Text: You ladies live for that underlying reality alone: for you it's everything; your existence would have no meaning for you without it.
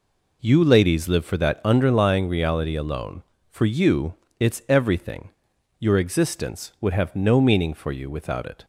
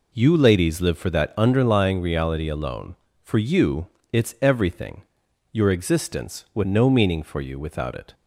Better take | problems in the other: first | pauses between "you" and "it's"; slight; at 3.8 s; 0.26 s long; slight in the first // skips "have"; at 6.6 s

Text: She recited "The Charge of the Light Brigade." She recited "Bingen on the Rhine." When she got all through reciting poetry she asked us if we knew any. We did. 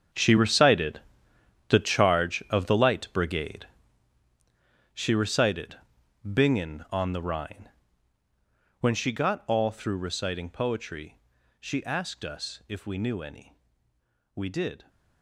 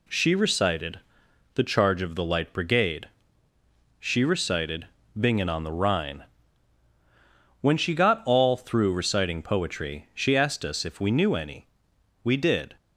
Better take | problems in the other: second | gets quieter; strong; throughout; 14.5 dB // pauses between "recited" and "The"; noticeable; at 1.0 s; 0.68 s long; noticeable in the second // pauses between "recited" and "Bingen"; noticeable; at 5.7 s; 0.48 s long; slight in the second // pauses between "poetry" and "she"; at 11.1 s; 0.42 s long

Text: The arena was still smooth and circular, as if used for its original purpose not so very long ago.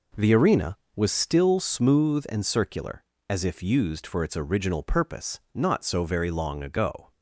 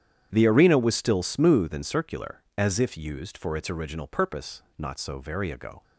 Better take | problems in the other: first | starts louder than the rest; strong; until 1.3 s; 9.5 dB // pauses between "purpose" and "not"; slight; at 4.6 s; 0.16 s long; slight in the first // skips "long"; at 5.5 s

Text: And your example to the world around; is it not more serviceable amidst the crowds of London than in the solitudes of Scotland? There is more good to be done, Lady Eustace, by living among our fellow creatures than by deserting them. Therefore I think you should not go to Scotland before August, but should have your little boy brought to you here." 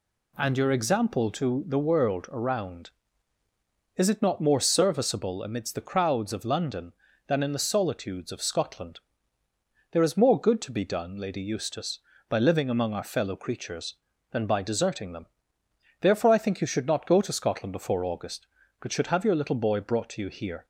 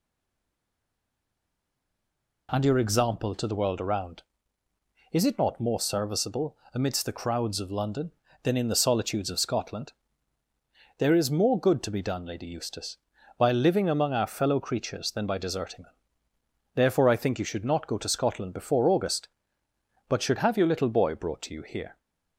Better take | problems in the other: first | stays silent before the first word; until 2.4 s; 2.4 s long // pauses between "serviceable" and "amidst"; slight; at 6.5 s; 0.18 s long

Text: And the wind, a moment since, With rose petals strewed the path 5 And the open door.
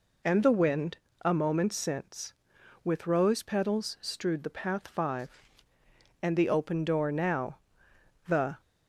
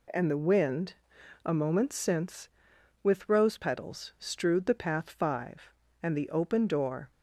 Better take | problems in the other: second | goes on to say "Now the"; from 7.0 s on; 1.5 s long

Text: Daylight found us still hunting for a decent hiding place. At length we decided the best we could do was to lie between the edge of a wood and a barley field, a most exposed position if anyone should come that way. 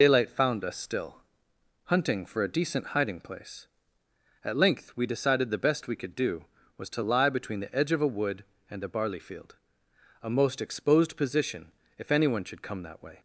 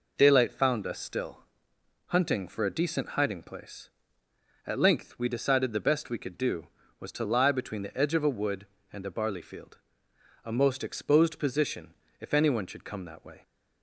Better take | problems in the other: second | loses the start of "Daylight"; at 0.0 s; 45 ms // pauses between "still" and "hunting"; noticeable; at 1.1 s; 0.66 s long; noticeable in the second // pauses between "position" and "if"; slight; at 11.6 s; 0.26 s long; slight in the second

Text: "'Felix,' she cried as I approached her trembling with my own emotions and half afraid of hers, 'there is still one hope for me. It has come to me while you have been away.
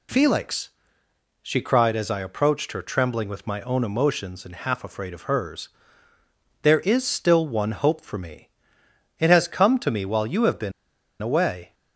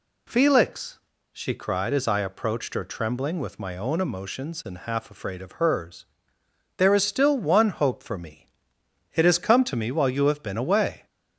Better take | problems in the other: second | pauses between "been" and "away"; noticeable; at 10.7 s; 0.50 s long

